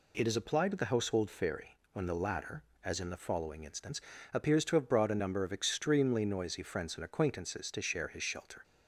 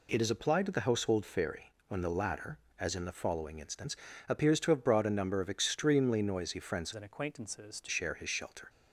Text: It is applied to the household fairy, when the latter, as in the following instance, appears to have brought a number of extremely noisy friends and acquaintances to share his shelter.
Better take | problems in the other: first | changes voice from "and" to "to"; from 6.9 to 7.8 s; 0.9 s long

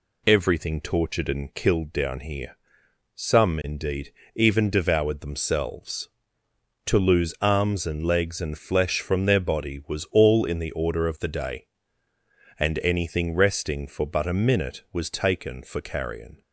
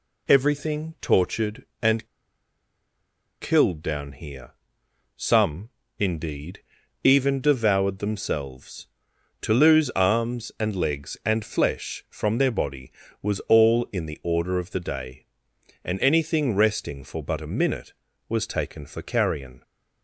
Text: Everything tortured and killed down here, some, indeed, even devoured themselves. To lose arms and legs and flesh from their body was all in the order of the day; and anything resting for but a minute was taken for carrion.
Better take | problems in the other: first | pauses between "and" and "killed"; strong; at 2.0 s; 1.3 s long

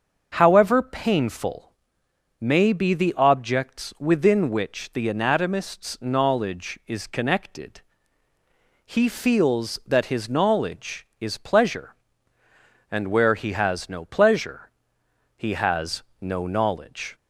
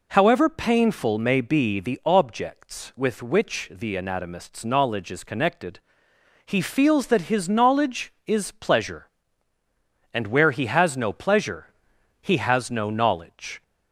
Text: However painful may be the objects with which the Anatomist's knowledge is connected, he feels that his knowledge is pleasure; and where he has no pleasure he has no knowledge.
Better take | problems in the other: second | starts louder than the rest; until 1.3 s; 6.5 dB // pauses between "painful" and "may"; noticeable; at 1.7 s; 0.68 s long // says "within" for "with"; at 3.9 s // pauses between "pleasure" and "he"; noticeable; at 14.7 s; 0.66 s long; noticeable in the second // pauses between "has" and "no"; slight; at 16.0 s; 0.18 s long

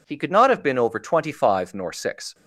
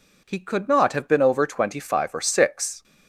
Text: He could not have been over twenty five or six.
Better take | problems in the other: second | says "nor" for "or"; at 1.7 s

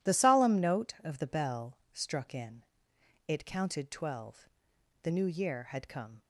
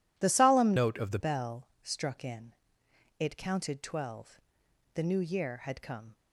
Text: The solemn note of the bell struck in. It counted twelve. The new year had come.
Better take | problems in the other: first | changes voice from "note" to "the"; from 0.7 to 1.1 s; 0.4 s long // pauses between "bell" and "struck"; slight; at 1.6 s; 0.16 s long; slight in the first

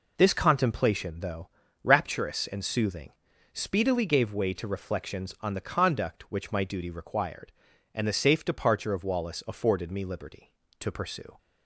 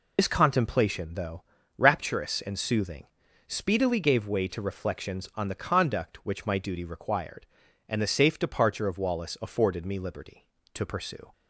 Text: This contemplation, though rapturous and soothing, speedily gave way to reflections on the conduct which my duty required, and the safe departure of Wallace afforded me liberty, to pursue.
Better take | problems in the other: first | loses the start of "This"; at 0.1 s; 70 ms // pauses between "though" and "rapturous"; slight; at 1.4 s; 0.36 s long; slight in the first

